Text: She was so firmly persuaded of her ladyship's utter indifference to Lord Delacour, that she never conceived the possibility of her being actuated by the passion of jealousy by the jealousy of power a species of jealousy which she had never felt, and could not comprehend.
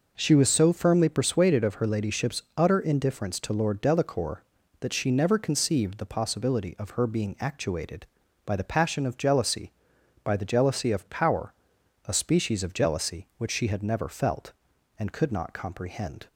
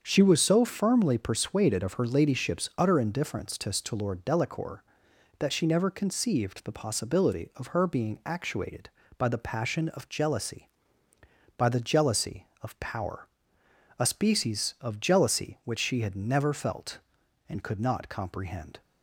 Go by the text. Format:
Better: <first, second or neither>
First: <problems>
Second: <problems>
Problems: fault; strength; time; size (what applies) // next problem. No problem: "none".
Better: first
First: pauses between "power" and "a"; noticeable; at 11.5 s; 0.54 s long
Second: starts louder than the rest; until 1.0 s; 7 dB // says "to" twice; at 3.7 s // pauses between "power" and "a"; noticeable; at 13.2 s; 0.70 s long